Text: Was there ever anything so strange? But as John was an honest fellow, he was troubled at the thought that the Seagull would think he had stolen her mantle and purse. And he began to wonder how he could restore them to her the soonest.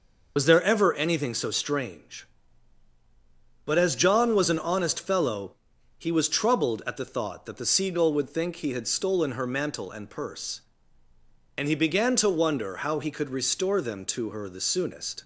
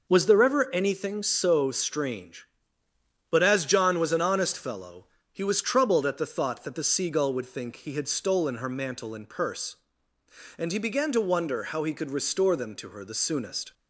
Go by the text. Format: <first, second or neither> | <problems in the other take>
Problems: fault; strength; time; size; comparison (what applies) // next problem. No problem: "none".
second | loses the start of "Was"; at 0.3 s; 50 ms